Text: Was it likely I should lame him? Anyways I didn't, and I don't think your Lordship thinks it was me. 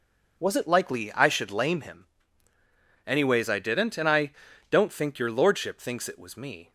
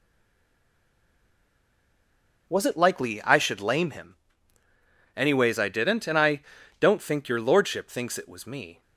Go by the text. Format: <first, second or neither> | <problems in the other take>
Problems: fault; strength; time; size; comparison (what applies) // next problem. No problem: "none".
first | stays silent before the first word; until 2.4 s; 2.4 s long // pauses between "I" and "don't"; at 6.4 s; 0.38 s long; also in the first